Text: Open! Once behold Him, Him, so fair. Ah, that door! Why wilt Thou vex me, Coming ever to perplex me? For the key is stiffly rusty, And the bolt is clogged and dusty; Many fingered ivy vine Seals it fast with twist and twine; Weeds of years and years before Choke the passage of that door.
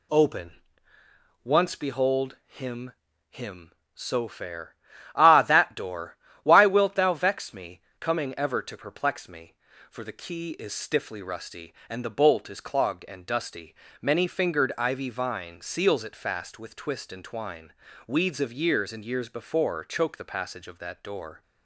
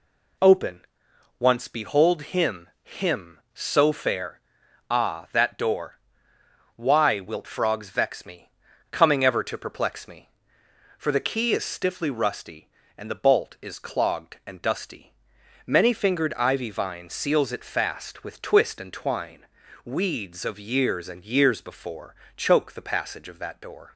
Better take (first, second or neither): first